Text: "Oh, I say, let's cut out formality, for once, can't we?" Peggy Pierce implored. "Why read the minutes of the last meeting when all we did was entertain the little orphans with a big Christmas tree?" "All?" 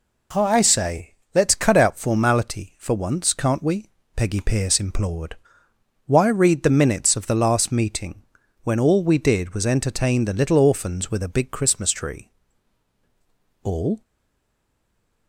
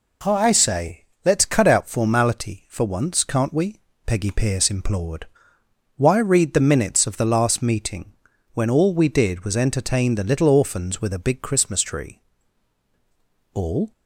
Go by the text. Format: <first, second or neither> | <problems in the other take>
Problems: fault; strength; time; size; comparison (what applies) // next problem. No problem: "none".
second | pauses between "meeting" and "when"; at 8.2 s; 0.42 s long; also in the second // stays silent after the last word; noticeable; from 14.0 s on; 1.2 s long